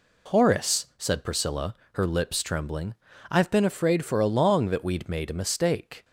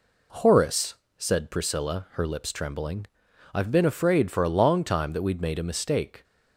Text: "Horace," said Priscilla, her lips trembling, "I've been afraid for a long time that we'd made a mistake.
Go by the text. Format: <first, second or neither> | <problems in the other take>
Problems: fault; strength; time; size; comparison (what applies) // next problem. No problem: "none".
second | skips "time"; at 4.7 s